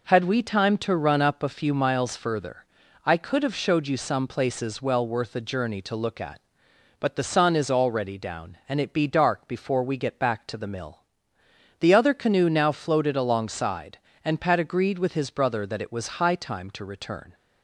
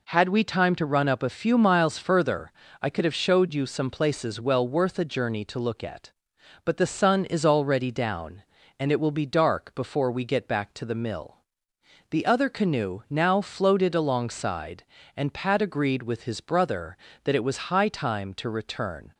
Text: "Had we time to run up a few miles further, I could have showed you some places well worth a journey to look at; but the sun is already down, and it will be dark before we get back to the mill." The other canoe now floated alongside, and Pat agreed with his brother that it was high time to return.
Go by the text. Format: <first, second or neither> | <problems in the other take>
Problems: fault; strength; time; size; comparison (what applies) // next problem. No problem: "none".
second | skips "will"; at 8.9 s